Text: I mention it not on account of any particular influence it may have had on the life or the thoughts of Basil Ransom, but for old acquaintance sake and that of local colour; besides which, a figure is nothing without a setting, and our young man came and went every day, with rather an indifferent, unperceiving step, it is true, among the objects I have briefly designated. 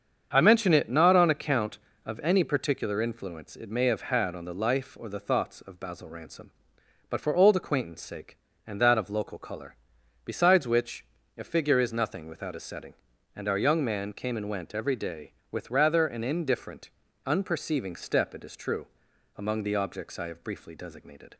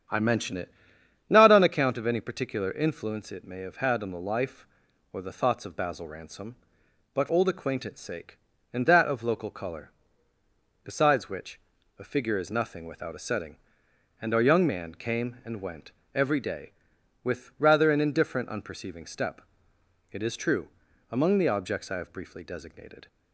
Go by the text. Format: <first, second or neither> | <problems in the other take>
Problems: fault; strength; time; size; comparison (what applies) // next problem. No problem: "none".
first | starts louder than the rest; strong; until 1.6 s; 8.5 dB; strong in the first // pauses between "it" and "not"; noticeable; at 0.7 s; 0.56 s long // skips "for"; at 7.2 s // pauses between "went" and "every"; slight; at 15.9 s; 0.22 s long